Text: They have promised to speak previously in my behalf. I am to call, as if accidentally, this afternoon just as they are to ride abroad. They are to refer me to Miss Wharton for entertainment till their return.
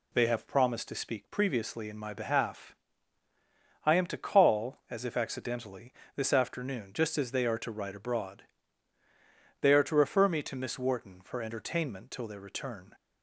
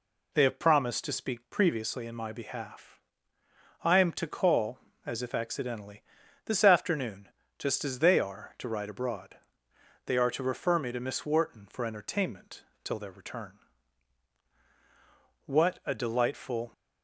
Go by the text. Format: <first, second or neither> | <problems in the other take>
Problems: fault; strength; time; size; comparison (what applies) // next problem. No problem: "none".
first | pauses between "afternoon" and "just"; slight; at 7.2 s; 0.30 s long // pauses between "entertainment" and "till"; slight; at 12.6 s; 0.22 s long // goes on to say "What a delightful"; noticeable; from 15.4 s on; 1.2 s long